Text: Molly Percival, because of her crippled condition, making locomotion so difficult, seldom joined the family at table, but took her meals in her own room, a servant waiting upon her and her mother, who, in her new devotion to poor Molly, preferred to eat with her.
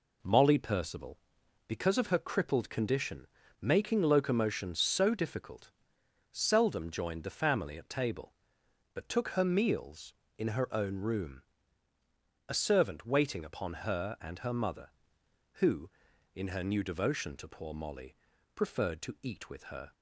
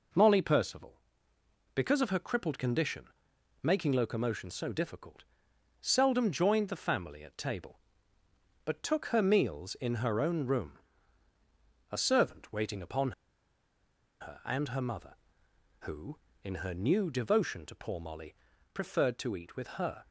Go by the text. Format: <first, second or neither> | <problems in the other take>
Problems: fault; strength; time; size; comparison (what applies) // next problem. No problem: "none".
first | pauses between "upon" and "her"; at 13.1 s; 1.0 s long